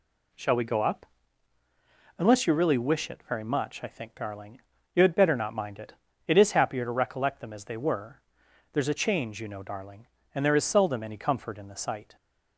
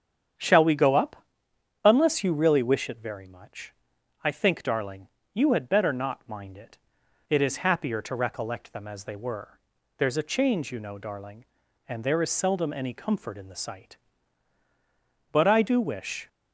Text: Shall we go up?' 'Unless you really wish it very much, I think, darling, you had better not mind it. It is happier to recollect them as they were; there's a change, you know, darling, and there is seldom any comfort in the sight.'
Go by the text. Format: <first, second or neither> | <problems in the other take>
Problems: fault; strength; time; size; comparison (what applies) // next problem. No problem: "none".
first | starts louder than the rest; strong; until 2.0 s; 8 dB // goes on to say "But I do wish"; noticeable; from 15.3 s on; 0.96 s long